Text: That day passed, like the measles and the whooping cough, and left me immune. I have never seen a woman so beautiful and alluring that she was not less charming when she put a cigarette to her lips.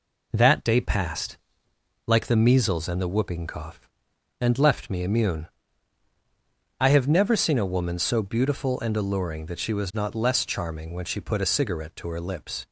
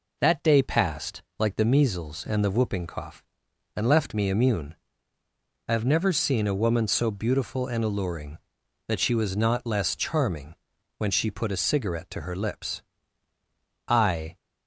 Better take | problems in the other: first | pauses between "charming" and "when"; at 10.5 s; 0.44 s long // goes on to say "I"; slight; from 13.8 s on; 0.48 s long

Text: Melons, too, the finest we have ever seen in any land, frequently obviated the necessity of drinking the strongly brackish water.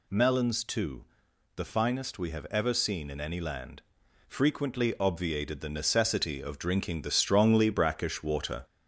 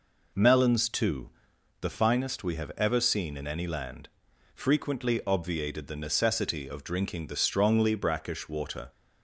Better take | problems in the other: second | gets louder; slight; throughout; 2.5 dB

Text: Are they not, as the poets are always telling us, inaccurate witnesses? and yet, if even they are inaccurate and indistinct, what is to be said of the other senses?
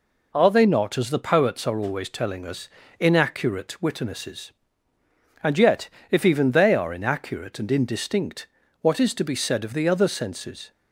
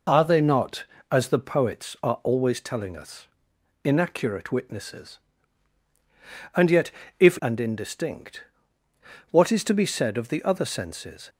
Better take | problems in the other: first | skips "even they are inaccurate"; at 7.3 s

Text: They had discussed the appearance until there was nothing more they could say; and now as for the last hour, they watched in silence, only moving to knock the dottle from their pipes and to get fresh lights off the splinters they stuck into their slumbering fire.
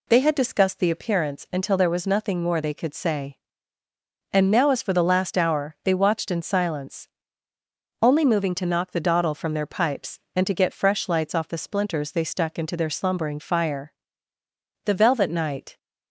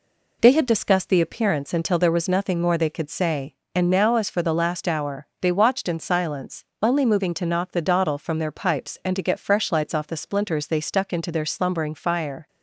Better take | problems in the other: second | goes on to say "The velvet night"; noticeable; from 14.8 s on; 0.92 s long

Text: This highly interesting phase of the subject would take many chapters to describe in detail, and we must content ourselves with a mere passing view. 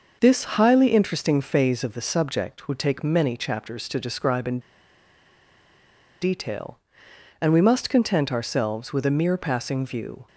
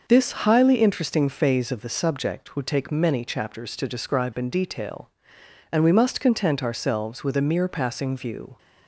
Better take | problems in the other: second | pauses between "in" and "detail"; strong; at 4.5 s; 1.6 s long

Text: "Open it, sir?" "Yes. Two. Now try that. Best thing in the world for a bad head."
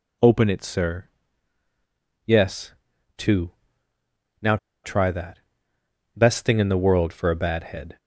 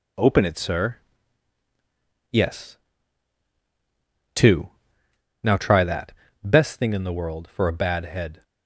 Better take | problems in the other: second | pauses between "Now" and "try"; slight; at 4.5 s; 0.27 s long

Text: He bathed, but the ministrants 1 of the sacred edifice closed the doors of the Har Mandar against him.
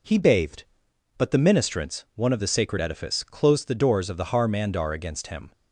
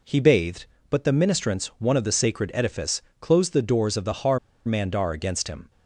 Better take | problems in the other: first | pauses between "edifice" and "closed"; slight; at 3.0 s; 0.20 s long // pauses between "Har" and "Mandar"; slight; at 4.3 s; 0.29 s long

